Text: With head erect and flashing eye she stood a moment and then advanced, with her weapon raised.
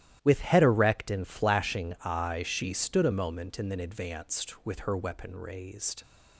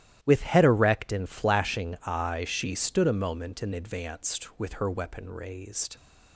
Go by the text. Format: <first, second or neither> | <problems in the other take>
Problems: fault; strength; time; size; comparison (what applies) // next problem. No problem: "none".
first | starts louder than the rest; strong; until 1.2 s; 13 dB; strong in the first // skips "then"; at 3.7 s